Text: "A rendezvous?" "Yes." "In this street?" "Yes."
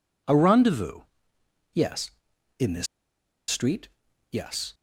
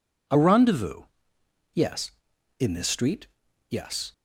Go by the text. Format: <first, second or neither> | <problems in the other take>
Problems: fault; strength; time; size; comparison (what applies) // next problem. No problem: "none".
second | pauses between "this" and "street"; noticeable; at 2.8 s; 0.63 s long